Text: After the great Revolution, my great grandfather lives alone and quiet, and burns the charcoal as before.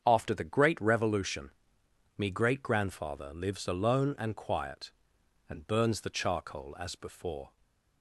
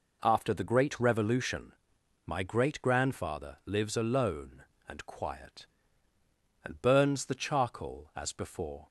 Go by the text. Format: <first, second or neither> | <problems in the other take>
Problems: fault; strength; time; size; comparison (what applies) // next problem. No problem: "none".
second | starts louder than the rest; strong; until 1.0 s; 7.5 dB // says "me" for "my"; at 2.1 s // stays silent after the last word; slight; from 7.4 s on; 0.6 s long